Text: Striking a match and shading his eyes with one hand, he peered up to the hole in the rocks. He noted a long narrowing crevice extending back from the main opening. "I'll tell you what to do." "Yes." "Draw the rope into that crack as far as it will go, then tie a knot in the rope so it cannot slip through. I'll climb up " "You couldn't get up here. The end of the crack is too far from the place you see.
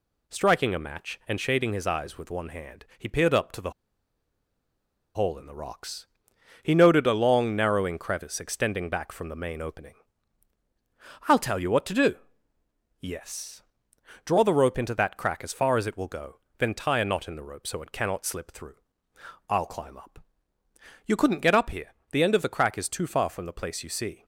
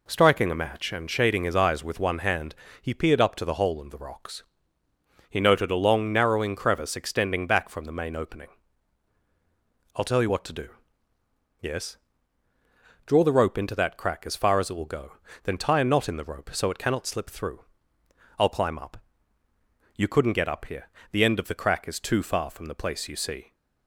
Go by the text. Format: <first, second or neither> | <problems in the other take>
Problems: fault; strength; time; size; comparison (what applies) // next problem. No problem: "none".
second | pauses between "the" and "hole"; strong; at 3.7 s; 1.4 s long